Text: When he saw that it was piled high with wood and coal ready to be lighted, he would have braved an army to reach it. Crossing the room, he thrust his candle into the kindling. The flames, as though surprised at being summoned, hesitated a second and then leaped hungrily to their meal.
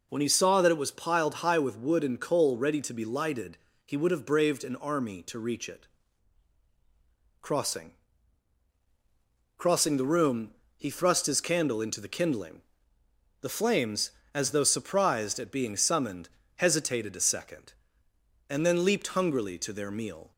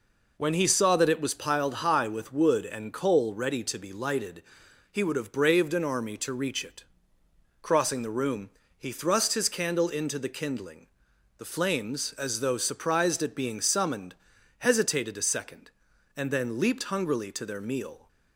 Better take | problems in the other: second | says "Crossing" twice; at 9.5 s

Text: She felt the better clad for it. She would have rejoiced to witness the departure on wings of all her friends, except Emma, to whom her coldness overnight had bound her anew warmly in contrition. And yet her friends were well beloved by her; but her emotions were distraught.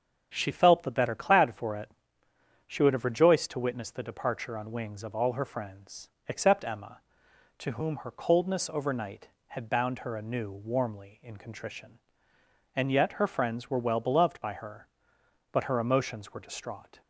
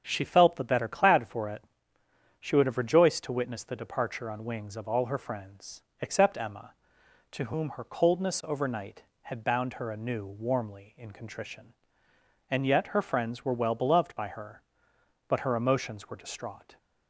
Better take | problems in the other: neither | starts louder than the rest; strong; the same in both

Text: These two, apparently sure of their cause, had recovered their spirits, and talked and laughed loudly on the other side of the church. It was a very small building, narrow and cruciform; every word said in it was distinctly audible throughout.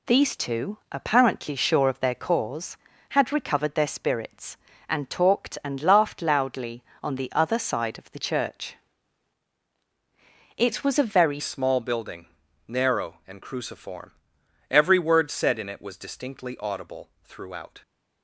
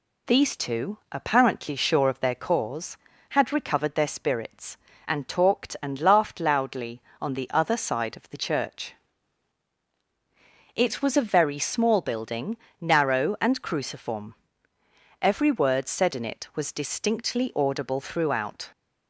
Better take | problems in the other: second | changes voice at "small"; from 11.3 s on; 6.5 s long

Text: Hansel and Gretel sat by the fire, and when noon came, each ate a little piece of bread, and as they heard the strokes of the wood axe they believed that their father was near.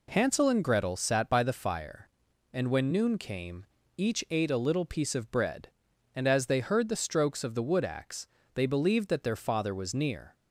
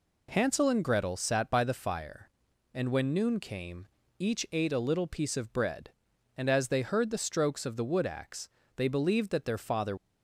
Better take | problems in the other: first | pauses between "axe" and "they"; slight; at 8.4 s; 0.28 s long; slight in the first // stops before "was near"; at 9.9 s

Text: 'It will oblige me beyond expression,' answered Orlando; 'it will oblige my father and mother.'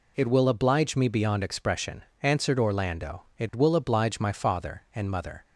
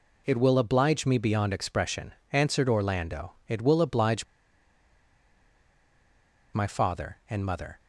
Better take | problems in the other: first | pauses between "oblige" and "my"; strong; at 4.2 s; 2.2 s long

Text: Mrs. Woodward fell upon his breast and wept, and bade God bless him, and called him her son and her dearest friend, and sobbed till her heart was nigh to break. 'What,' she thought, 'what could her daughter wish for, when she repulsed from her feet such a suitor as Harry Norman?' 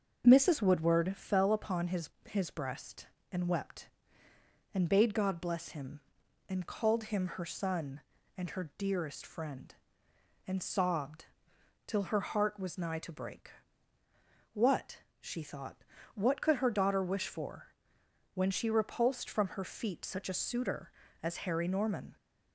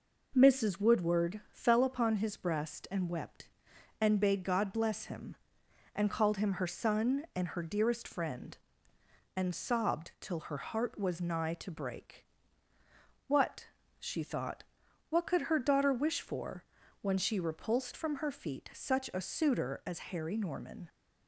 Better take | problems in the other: second | starts louder than the rest; noticeable; until 1.2 s; 6 dB // says "his" twice; at 2.2 s // pauses between "sobbed" and "till"; noticeable; at 11.2 s; 0.60 s long

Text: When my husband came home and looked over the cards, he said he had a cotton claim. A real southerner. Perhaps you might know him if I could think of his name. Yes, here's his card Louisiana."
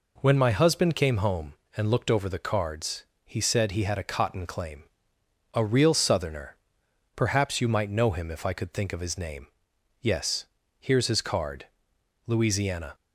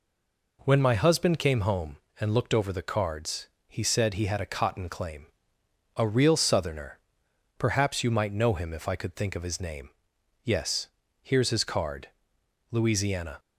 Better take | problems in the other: first | stays silent before the first word; slight; until 0.5 s; 0.5 s long // pauses between "card" and "Louisiana"; noticeable; at 12.0 s; 0.62 s long; noticeable in the first

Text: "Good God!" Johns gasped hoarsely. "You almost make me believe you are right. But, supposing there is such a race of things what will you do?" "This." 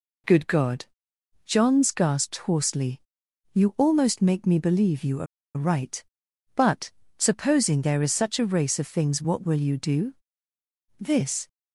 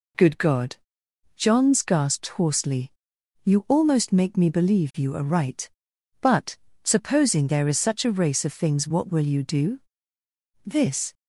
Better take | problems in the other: second | pauses between "are" and "right"; slight; at 5.2 s; 0.31 s long

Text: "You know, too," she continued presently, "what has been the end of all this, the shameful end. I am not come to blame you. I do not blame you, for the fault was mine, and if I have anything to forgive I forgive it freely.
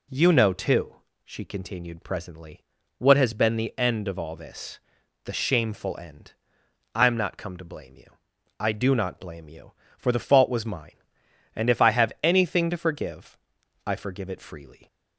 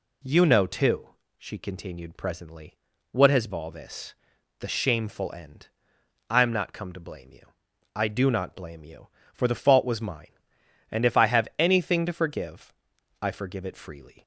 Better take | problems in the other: first | skips "been the end of"; at 3.5 s // pauses between "forgive" and "I"; noticeable; at 12.7 s; 0.48 s long; noticeable in the first

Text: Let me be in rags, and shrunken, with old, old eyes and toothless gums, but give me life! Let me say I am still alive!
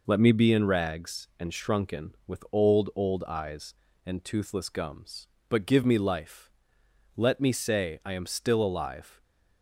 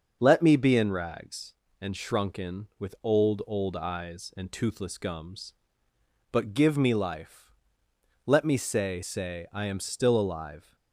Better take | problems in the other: first | starts louder than the rest; until 1.2 s; 6.5 dB // says "say" twice; at 9.0 s

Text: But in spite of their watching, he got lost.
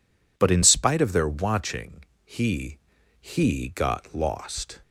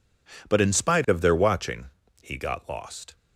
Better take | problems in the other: second | says "he" twice; at 3.2 s

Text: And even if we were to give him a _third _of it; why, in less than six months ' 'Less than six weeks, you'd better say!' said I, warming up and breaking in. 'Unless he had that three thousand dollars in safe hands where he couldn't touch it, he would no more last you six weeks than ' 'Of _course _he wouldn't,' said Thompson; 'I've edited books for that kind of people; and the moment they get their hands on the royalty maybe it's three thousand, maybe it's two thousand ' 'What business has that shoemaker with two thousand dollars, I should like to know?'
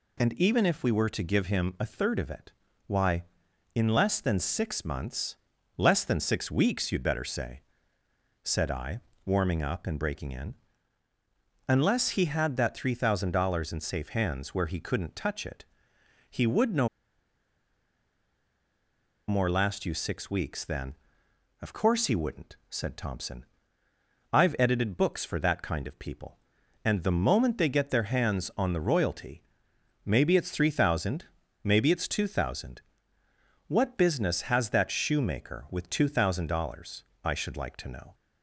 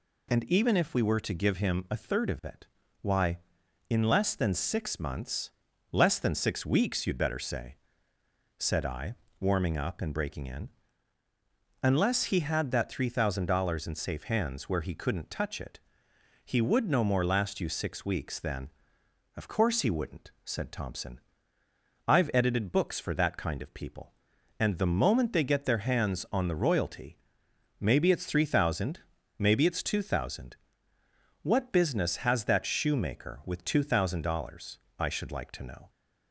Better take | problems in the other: second | pauses between "no" and "more"; strong; at 16.8 s; 2.4 s long // pauses between "royalty" and "maybe"; noticeable; at 29.4 s; 0.62 s long; noticeable in the second

